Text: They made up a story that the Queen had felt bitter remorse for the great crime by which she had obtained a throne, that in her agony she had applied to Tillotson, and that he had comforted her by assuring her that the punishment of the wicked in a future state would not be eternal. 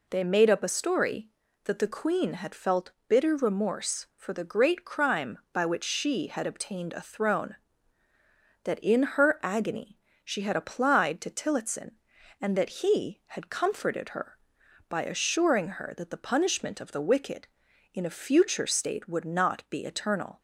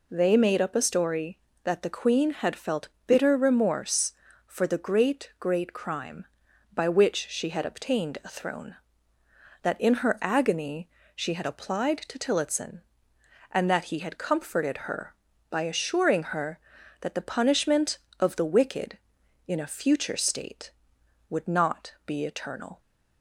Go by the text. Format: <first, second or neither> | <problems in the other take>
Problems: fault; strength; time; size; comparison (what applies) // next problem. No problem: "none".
first | pauses between "felt" and "bitter"; slight; at 2.8 s; 0.18 s long; slight in the first // says "great" twice; at 5.3 s // pauses between "agony" and "she"; slight; at 10.8 s; 0.28 s long; slight in the first